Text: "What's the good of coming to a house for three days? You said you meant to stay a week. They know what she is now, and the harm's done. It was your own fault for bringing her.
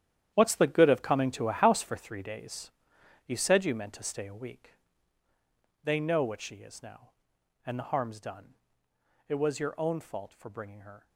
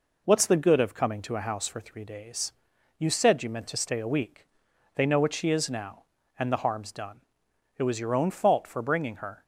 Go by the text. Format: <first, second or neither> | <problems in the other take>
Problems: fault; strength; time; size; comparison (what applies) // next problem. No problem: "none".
second | gets quieter; strong; throughout; 13 dB